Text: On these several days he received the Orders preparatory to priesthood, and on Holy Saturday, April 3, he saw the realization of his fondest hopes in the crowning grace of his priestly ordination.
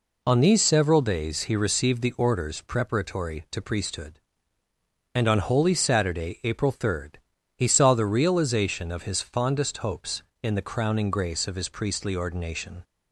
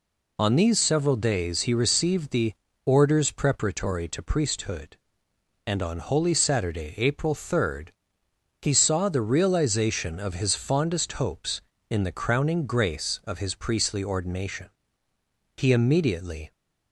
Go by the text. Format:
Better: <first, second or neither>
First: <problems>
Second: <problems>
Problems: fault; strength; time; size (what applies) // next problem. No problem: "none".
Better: first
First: none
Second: pauses between "the" and "Orders"; slight; at 2.5 s; 0.32 s long // goes on to say "He immediately"; noticeable; from 15.5 s on; 0.96 s long